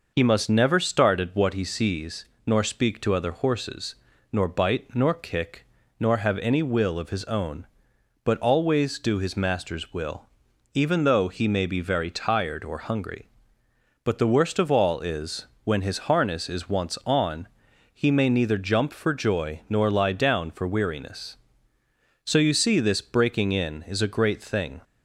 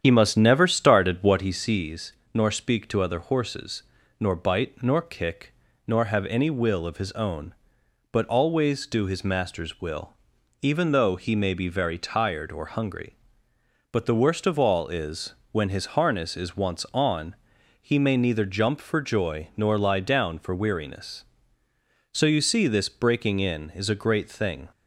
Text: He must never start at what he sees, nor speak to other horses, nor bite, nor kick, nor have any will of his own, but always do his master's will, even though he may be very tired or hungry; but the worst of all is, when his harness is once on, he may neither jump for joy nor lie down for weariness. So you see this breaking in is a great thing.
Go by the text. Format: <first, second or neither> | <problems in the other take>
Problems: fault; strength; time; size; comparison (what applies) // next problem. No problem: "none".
first | starts louder than the rest; strong; until 1.7 s; 9 dB